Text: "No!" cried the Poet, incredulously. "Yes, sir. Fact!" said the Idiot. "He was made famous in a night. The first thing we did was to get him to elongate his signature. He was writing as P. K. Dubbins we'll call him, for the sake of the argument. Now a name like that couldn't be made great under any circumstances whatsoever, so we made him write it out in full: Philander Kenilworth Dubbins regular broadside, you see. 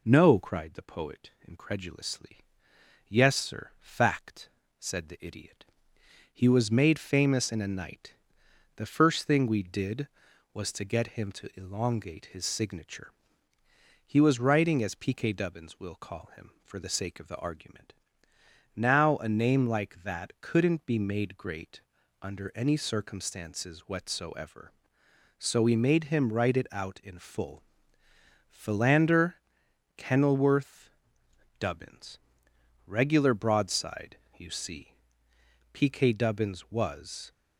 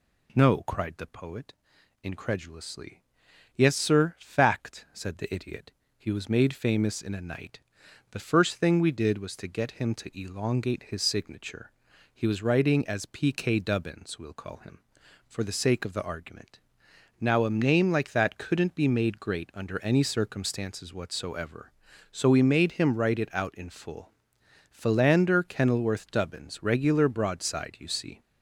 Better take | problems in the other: second | pauses between "great" and "under"; at 21.8 s; 0.40 s long // pauses between "Philander" and "Kenilworth"; noticeable; at 29.3 s; 0.62 s long // pauses between "Kenilworth" and "Dubbins"; noticeable; at 30.8 s; 0.70 s long // pauses between "Dubbins" and "regular"; noticeable; at 32.1 s; 0.70 s long // goes on to say "P K Dubbins was"; from 35.7 s on; 1.5 s long

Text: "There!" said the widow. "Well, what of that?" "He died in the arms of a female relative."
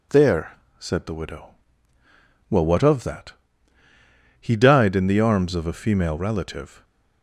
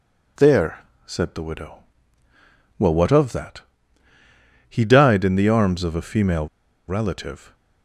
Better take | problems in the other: first | pauses between "female" and "relative"; at 6.4 s; 0.42 s long

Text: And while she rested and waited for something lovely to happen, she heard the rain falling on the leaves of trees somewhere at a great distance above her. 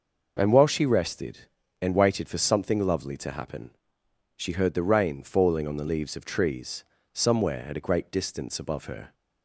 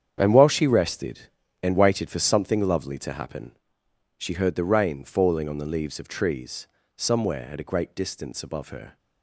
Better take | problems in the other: first | gets quieter; strong; throughout; 12 dB // pauses between "trees" and "somewhere"; slight; at 6.6 s; 0.30 s long; slight in the first

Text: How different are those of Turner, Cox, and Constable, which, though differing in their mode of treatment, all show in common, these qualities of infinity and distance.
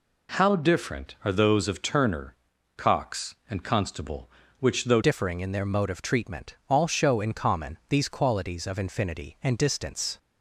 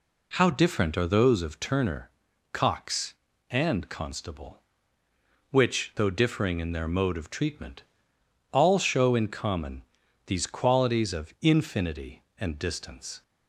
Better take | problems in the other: second | changes voice at "differing"; from 5.0 s on; 5.1 s long

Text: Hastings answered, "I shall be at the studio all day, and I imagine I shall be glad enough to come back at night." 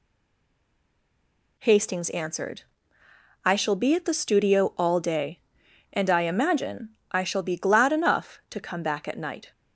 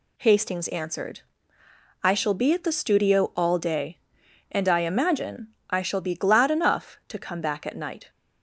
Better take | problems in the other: second | stays silent before the first word; noticeable; until 1.5 s; 1.5 s long // pauses between "imagine" and "I"; slight; at 6.8 s; 0.20 s long; slight in the second

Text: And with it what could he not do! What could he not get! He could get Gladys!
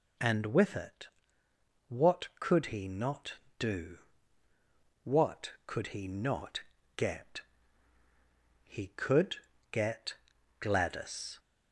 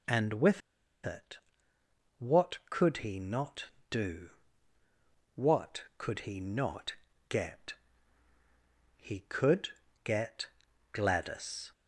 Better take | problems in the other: first | pauses between "with" and "it"; at 0.6 s; 0.45 s long // pauses between "it" and "what"; noticeable; at 1.3 s; 0.82 s long; noticeable in the first // pauses between "not" and "get"; slight; at 6.9 s; 0.36 s long; slight in the first // pauses between "could" and "get"; slight; at 9.6 s; 0.34 s long; slight in the first // pauses between "get" and "Gladys"; at 10.4 s; 0.44 s long; also in the first

